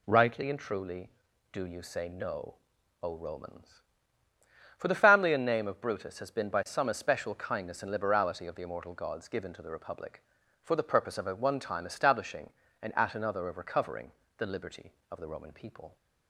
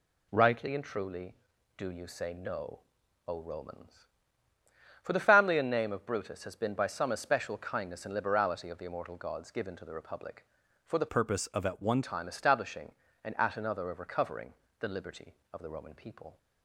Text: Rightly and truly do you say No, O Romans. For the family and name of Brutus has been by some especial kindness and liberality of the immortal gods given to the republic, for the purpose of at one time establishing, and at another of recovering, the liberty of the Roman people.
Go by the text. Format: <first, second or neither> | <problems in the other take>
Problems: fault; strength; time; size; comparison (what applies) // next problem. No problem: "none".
first | changes voice from "purpose" to "one"; from 11.0 to 12.0 s; 1.0 s long